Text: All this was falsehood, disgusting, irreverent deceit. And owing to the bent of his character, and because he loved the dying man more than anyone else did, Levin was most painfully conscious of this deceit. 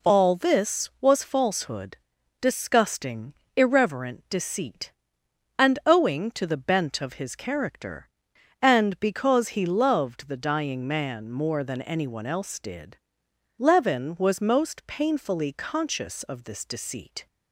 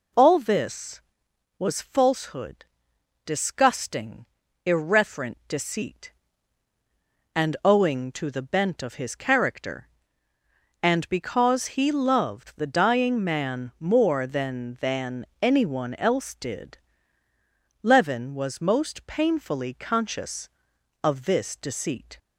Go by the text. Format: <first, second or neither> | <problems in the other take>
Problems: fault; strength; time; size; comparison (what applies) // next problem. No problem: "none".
first | says "than" twice; at 14.8 s